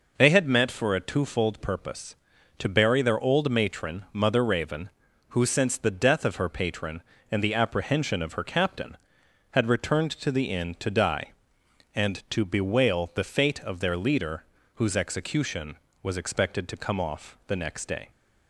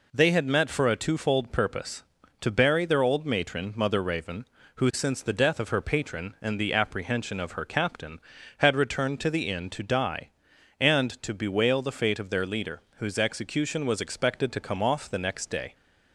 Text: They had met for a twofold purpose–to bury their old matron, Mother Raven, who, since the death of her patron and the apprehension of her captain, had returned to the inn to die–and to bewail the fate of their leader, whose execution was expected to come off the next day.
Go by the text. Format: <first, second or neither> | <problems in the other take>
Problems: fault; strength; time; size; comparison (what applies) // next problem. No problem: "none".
neither | none